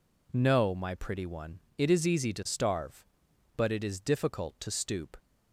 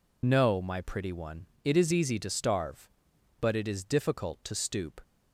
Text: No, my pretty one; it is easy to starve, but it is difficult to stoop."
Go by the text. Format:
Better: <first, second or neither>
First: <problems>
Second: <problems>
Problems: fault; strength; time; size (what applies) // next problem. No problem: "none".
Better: first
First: none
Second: loses the start of "No"; at 0.2 s; 70 ms